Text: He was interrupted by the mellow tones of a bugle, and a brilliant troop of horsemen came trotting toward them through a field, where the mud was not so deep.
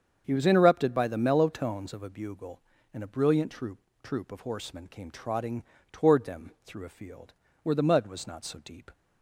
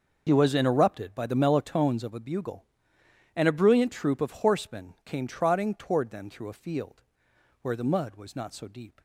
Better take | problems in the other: second | starts louder than the rest; strong; until 1.2 s; 7.5 dB // says "troop" twice; at 4.0 s // pauses between "trotting" and "toward"; slight; at 5.6 s; 0.31 s long

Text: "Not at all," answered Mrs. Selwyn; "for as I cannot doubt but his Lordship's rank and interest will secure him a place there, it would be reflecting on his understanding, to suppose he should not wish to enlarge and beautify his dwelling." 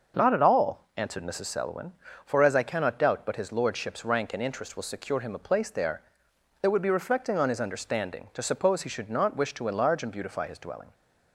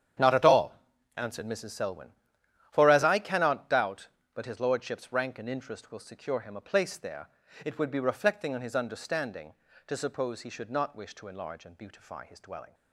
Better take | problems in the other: first | gets quieter; strong; throughout; 13.5 dB // starts louder than the rest; strong; until 1.6 s; 9 dB; also in the first

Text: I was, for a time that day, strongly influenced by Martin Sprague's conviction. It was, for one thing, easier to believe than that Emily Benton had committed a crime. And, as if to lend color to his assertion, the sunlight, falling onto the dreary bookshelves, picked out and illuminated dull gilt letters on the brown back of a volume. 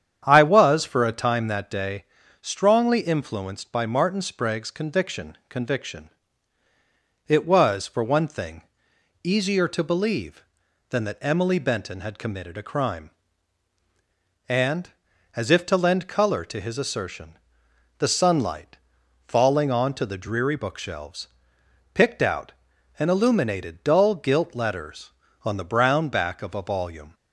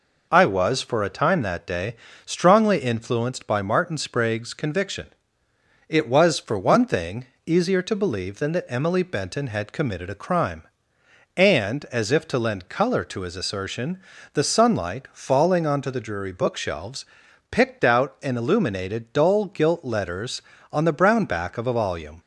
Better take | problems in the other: second | starts louder than the rest; strong; until 1.2 s; 8.5 dB // says "conviction" twice; at 5.4 s

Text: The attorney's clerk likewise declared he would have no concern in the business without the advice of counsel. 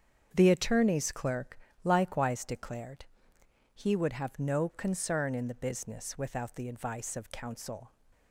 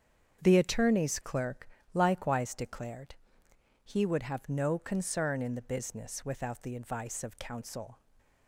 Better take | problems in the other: neither | starts louder than the rest; strong; the same in both // pauses between "clerk" and "likewise"; slight; the same in both // pauses between "declared" and "he"; noticeable; the same in both

